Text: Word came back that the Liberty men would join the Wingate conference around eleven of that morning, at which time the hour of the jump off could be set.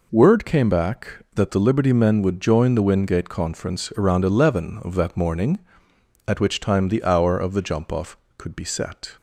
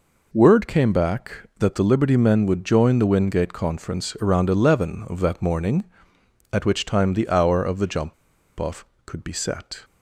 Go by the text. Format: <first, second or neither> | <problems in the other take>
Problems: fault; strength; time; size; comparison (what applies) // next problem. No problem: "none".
first | pauses between "jump" and "off"; noticeable; at 8.1 s; 0.45 s long